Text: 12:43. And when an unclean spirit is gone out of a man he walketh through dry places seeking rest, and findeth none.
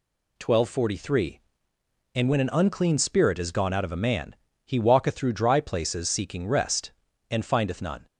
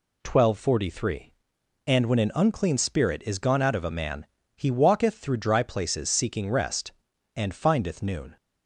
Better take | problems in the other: first | pauses between "man" and "he"; slight; at 4.2 s; 0.28 s long; slight in the first // says "noon" for "none"; at 8.0 s

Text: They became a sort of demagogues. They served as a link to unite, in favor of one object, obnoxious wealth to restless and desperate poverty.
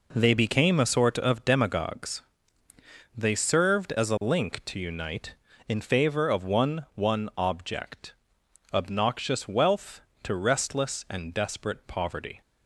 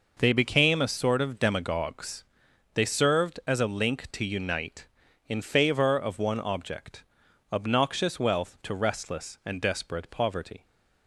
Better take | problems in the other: second | says "one" twice; at 6.9 s

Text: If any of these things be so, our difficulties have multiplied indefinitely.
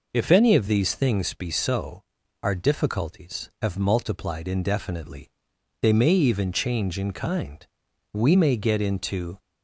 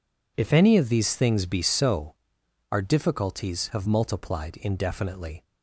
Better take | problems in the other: second | goes on to say "They may even change in kind We may get into"; strong; from 5.8 s on; 3.5 s long

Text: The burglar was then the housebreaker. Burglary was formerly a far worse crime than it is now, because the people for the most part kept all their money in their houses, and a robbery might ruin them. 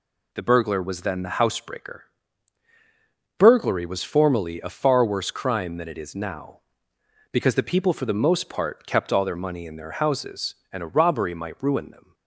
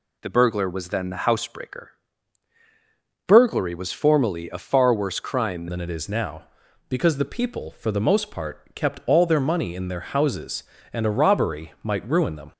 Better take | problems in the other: first | changes voice at "than"; from 5.6 s on; 6.9 s long

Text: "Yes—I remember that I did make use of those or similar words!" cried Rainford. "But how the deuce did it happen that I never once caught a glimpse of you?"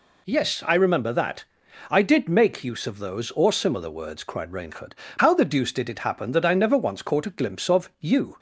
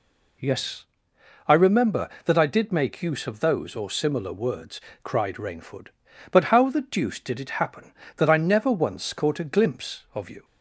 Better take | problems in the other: second | pauses between "that" and "I"; noticeable; at 1.4 s; 0.46 s long // skips "But"; at 5.0 s

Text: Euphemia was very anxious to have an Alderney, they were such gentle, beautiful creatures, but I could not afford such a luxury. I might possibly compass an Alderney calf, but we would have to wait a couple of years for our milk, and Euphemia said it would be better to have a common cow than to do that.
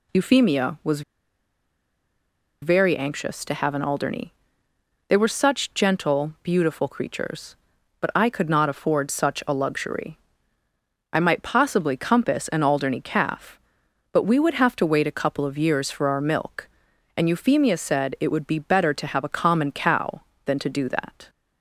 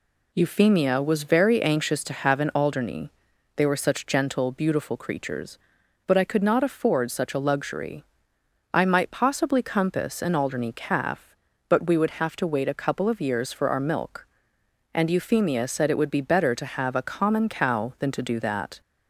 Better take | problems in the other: second | pauses between "was" and "very"; strong; at 1.0 s; 1.6 s long

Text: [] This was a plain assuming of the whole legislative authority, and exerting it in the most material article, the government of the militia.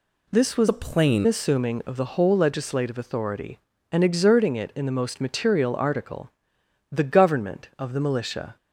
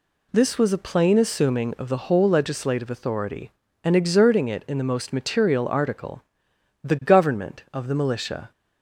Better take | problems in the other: second | changes voice from "a" to "plain"; from 0.6 to 1.2 s; 0.6 s long

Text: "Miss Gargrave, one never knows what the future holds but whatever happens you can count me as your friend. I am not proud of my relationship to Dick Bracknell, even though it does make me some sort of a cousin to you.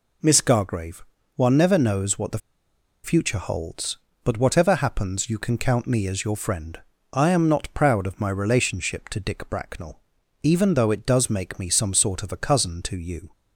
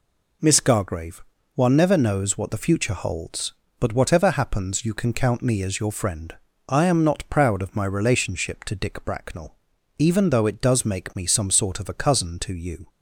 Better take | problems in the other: second | pauses between "the" and "future"; noticeable; at 2.3 s; 0.66 s long

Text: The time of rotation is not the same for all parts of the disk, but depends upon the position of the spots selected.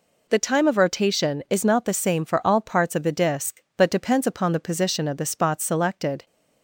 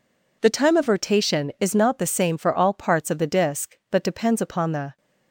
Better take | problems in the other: first | stops before "position of the spots selected"; at 4.9 s

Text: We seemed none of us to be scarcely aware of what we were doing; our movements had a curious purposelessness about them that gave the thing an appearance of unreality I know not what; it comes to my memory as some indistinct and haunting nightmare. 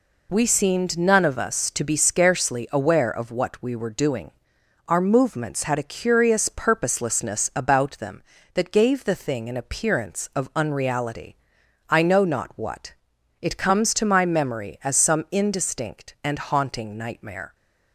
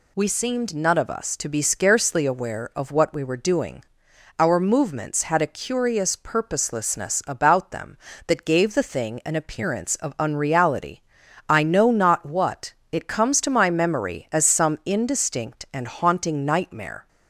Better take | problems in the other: neither | pauses between "unreality" and "I"; noticeable; the same in both

